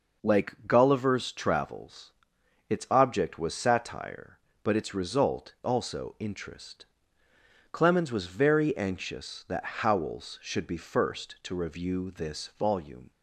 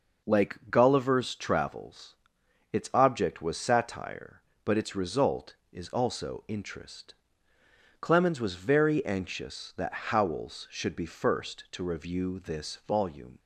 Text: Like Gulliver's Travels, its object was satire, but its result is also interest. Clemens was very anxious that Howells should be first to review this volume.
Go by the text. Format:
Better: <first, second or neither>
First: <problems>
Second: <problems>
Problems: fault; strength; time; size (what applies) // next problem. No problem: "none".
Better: second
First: skips "is"; at 5.5 s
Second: none